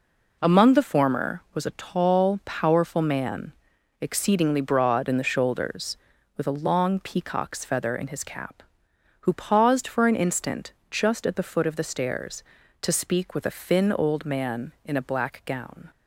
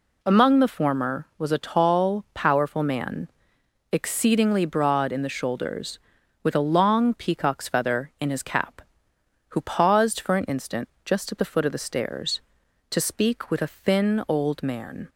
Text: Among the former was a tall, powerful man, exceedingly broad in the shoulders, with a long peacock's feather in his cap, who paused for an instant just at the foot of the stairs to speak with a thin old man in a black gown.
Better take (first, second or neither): first